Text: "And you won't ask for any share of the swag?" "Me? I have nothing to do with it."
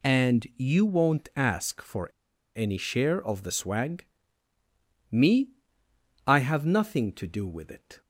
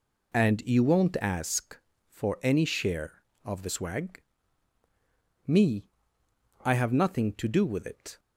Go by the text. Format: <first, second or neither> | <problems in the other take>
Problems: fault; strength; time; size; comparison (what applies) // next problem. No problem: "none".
second | pauses between "for" and "any"; noticeable; at 2.0 s; 0.47 s long